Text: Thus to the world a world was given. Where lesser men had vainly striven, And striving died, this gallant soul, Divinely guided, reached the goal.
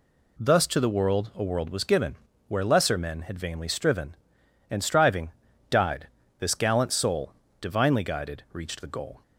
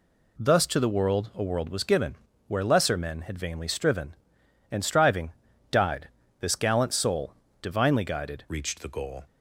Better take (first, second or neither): first